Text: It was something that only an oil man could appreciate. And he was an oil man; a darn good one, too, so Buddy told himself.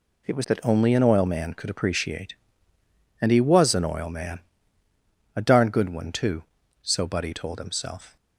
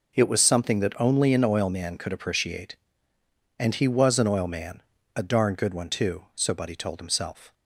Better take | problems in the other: second | skips "something"; at 0.4 s

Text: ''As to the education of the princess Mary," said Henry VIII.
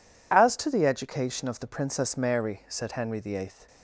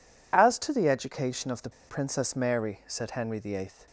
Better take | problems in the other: first | pauses between "the" and "princess"; slight; at 1.7 s; 0.18 s long

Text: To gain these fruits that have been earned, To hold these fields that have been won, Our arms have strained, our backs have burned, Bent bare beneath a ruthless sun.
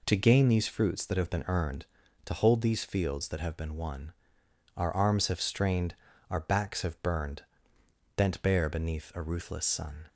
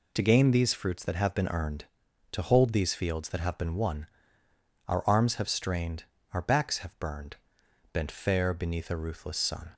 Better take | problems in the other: first | says "fair" for "bare"; at 8.1 s

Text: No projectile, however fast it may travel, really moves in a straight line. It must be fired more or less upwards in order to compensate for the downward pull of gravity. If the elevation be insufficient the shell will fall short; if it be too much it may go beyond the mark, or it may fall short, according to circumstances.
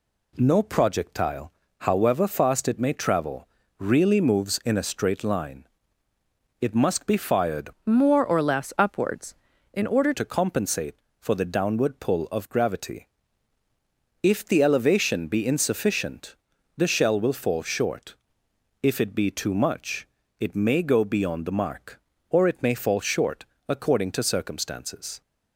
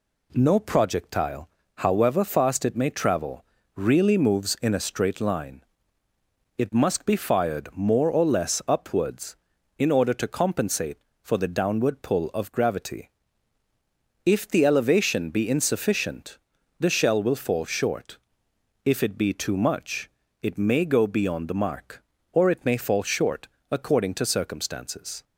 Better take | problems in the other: second | changes voice from "more" to "order"; from 7.8 to 10.1 s; 2.3 s long // pauses between "insufficient" and "the"; at 16.3 s; 0.42 s long; also in the second // pauses between "much" and "it"; slight; at 20.0 s; 0.32 s long; slight in the second

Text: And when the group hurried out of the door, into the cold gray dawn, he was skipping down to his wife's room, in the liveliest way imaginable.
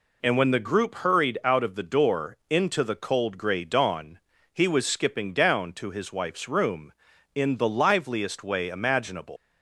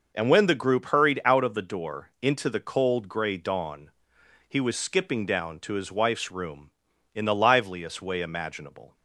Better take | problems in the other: second | leaves "imaginable" unfinished; at 9.3 s; 180 ms

